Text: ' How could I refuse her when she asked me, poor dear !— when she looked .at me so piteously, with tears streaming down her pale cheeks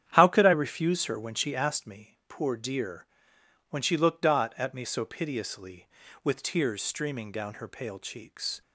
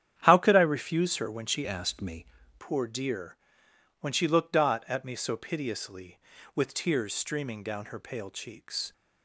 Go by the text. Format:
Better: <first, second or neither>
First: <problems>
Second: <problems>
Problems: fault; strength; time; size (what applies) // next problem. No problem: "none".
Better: first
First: starts louder than the rest; strong; until 1.1 s; 9.5 dB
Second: starts louder than the rest; strong; until 1.2 s; 9.5 dB // changes voice from "asked" to "me"; from 1.6 to 2.2 s; 0.6 s long